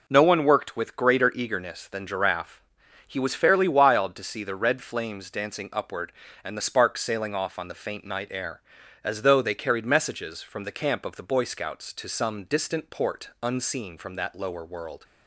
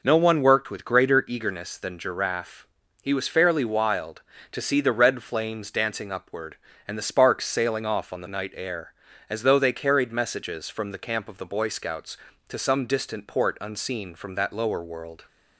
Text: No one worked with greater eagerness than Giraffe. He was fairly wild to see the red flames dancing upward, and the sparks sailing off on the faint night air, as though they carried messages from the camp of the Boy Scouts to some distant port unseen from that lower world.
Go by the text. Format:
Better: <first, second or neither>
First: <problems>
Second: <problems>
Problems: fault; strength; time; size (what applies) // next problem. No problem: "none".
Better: first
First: none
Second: skips "faint"; at 8.2 s